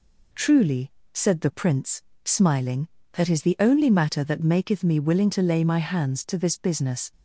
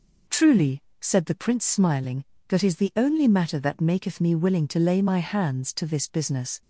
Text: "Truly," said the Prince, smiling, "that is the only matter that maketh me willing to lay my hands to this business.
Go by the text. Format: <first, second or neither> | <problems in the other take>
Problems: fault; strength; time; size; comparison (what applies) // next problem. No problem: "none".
neither | none